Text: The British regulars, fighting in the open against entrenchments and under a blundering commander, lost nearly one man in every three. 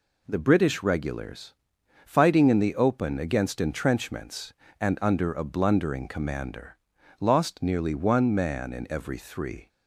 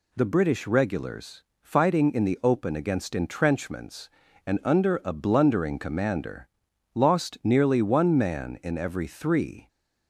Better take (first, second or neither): neither